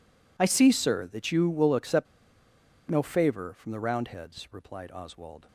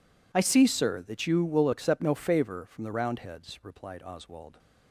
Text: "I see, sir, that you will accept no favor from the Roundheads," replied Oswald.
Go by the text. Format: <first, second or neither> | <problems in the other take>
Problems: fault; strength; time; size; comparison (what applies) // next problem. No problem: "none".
second | pauses between "accept" and "no"; noticeable; at 2.0 s; 0.85 s long